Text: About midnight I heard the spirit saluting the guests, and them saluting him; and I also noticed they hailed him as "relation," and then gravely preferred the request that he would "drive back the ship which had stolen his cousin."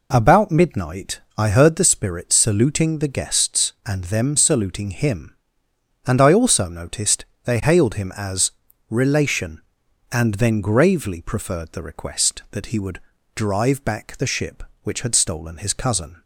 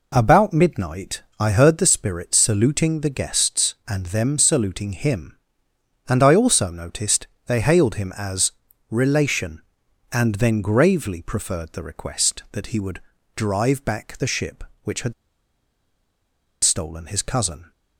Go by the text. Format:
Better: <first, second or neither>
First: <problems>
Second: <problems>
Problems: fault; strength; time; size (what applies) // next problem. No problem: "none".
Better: first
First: pauses between "midnight" and "I"; slight; at 1.2 s; 0.16 s long // pauses between "noticed" and "they"; slight; at 7.2 s; 0.22 s long // pauses between "as" and "relation"; at 8.5 s; 0.40 s long // pauses between "would" and "drive"; slight; at 13.0 s; 0.34 s long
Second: pauses between "midnight" and "I"; slight; at 1.2 s; 0.16 s long // pauses between "noticed" and "they"; slight; at 7.2 s; 0.22 s long // pauses between "as" and "relation"; at 8.5 s; 0.40 s long // pauses between "would" and "drive"; slight; at 13.0 s; 0.34 s long // pauses between "had" and "stolen"; strong; at 15.1 s; 1.5 s long